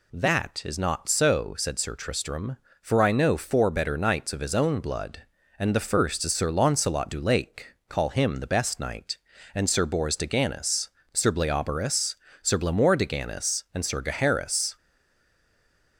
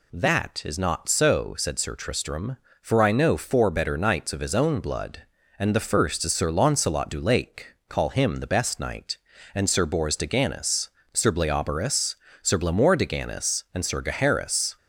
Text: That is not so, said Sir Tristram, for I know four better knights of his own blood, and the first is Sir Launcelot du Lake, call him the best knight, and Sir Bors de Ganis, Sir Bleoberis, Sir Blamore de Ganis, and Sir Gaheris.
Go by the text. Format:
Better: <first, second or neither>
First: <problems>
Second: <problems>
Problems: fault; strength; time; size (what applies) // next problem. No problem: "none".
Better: second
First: stays silent after the last word; noticeable; from 14.7 s on; 1.2 s long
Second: none